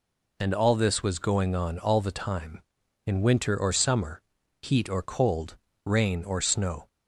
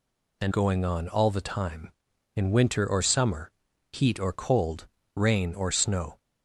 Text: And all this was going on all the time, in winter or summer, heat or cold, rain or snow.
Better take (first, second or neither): first